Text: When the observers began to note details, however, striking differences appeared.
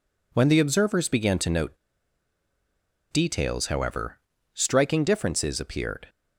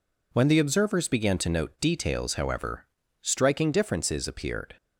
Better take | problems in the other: second | pauses between "note" and "details"; strong; at 1.7 s; 1.3 s long

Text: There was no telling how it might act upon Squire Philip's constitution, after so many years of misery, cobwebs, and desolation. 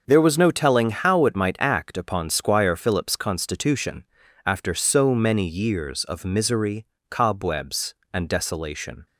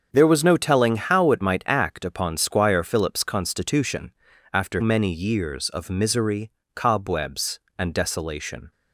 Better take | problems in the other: first | starts louder than the rest; until 1.1 s; 7 dB; noticeable in the first // skips "so"; at 4.8 s

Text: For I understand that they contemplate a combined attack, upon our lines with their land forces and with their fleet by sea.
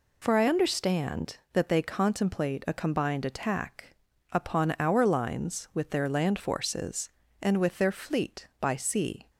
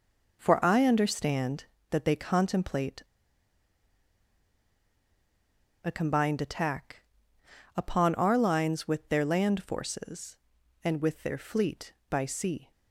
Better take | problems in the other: first | pauses between "contemplate" and "a"; strong; at 3.0 s; 2.8 s long

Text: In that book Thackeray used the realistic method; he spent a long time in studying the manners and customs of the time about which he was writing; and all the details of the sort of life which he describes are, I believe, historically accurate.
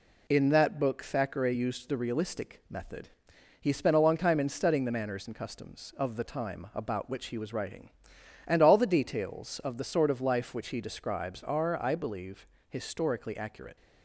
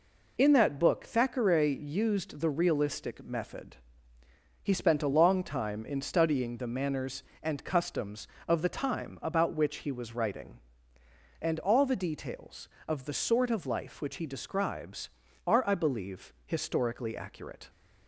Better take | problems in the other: neither | none

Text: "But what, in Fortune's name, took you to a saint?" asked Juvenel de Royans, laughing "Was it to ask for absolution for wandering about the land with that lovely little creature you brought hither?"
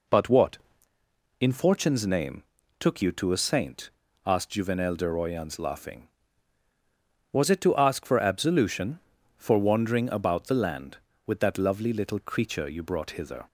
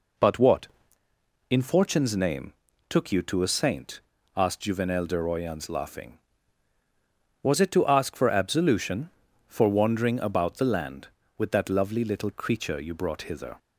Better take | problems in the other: neither | none

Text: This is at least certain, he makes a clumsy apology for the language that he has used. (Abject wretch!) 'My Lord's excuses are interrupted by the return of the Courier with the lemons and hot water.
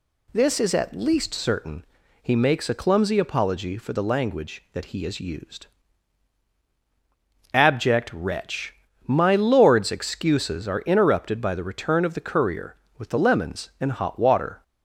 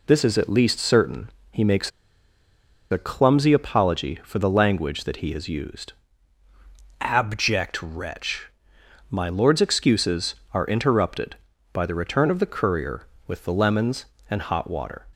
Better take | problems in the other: first | pauses between "makes" and "a"; at 1.9 s; 1.0 s long

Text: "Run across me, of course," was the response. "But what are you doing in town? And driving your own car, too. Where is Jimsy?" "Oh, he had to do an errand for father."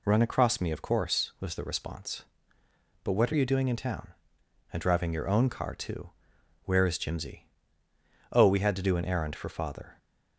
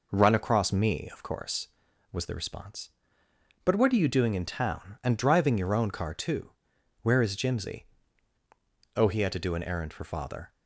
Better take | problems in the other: second | says "we" for "he"; at 8.4 s

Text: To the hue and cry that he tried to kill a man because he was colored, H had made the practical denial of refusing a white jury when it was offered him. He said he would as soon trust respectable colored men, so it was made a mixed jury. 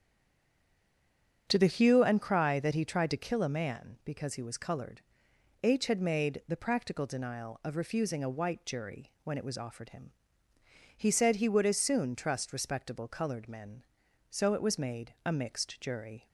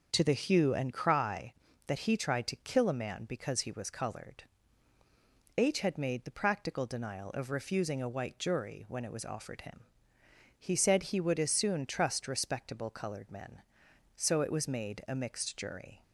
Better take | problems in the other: second | stays silent before the first word; noticeable; until 1.4 s; 1.4 s long // starts louder than the rest; strong; until 2.5 s; 8 dB; also in the second

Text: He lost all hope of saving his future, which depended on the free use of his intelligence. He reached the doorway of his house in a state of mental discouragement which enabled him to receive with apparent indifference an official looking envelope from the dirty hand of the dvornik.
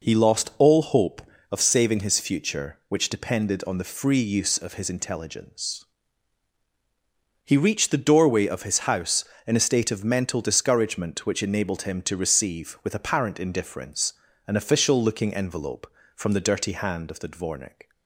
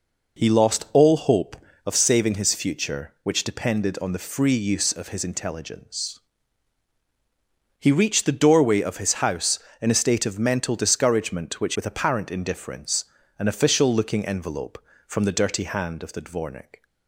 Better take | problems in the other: first | skips "enabled him to receive"; at 11.7 s // pauses between "indifference" and "an"; slight; at 13.0 s; 0.32 s long; slight in the first

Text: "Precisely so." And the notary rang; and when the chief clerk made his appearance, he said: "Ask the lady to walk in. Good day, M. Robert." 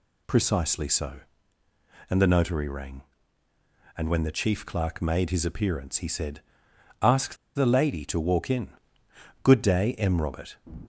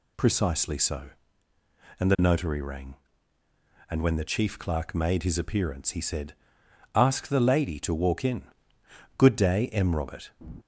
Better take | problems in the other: second | pauses between "Ask" and "the"; slight; at 7.3 s; 0.20 s long

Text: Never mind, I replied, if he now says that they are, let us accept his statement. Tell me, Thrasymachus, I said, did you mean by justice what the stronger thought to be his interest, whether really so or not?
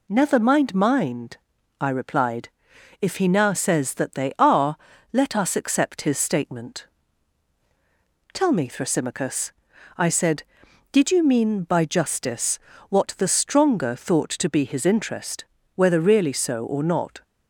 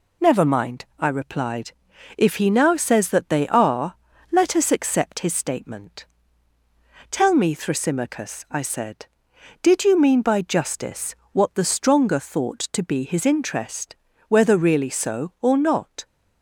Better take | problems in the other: second | says "mind" twice; at 0.7 s // pauses between "justice" and "what"; slight; at 12.5 s; 0.30 s long; slight in the second

